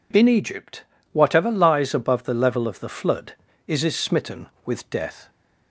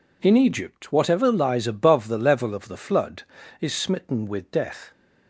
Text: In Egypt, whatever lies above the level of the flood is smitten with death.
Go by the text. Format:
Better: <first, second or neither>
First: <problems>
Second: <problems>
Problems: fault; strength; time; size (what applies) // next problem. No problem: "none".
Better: second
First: says "is" twice; at 3.8 s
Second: none